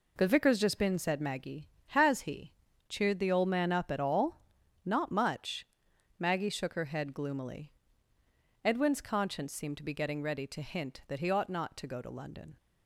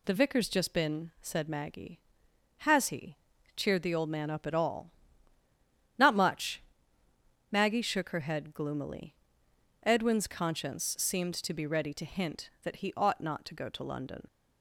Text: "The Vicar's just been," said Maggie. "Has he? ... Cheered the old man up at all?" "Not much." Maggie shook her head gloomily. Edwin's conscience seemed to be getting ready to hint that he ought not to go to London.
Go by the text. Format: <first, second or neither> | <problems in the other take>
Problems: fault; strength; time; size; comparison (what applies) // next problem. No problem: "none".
first | skips "getting"; at 11.6 s